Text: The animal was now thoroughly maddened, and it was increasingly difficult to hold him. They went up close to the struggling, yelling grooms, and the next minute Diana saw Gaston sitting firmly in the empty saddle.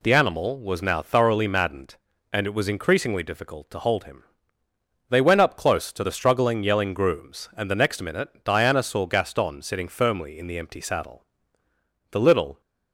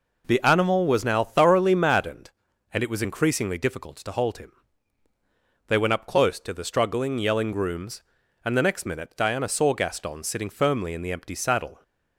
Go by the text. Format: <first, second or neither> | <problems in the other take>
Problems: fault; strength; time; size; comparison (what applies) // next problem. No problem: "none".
second | pauses between "minute" and "Diana"; slight; at 8.2 s; 0.16 s long // goes on to say "The little"; slight; from 12.1 s on; 0.48 s long